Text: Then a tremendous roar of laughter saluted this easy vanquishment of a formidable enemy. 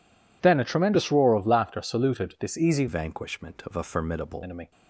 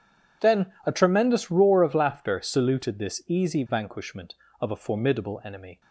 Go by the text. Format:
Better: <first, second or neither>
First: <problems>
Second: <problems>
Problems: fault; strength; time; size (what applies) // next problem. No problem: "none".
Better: second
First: changes voice from "vanquishment" to "formidable"; from 2.8 to 4.4 s; 1.6 s long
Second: none